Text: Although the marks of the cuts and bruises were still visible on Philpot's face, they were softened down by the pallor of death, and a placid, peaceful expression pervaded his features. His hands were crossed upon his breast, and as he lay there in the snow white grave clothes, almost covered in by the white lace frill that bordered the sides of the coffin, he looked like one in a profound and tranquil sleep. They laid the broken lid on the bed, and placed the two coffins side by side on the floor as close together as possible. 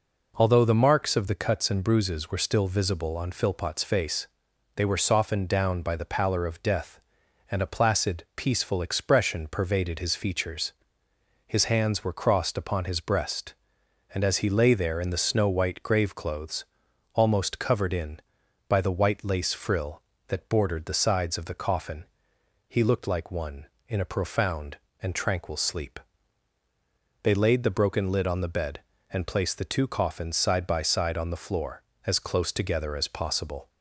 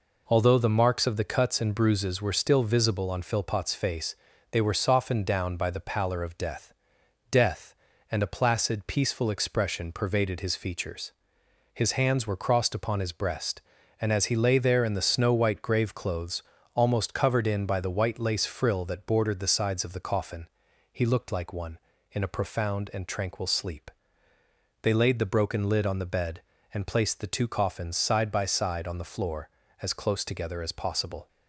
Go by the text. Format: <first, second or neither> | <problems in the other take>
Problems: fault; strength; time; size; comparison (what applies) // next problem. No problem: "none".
first | says "death" twice; at 7.3 s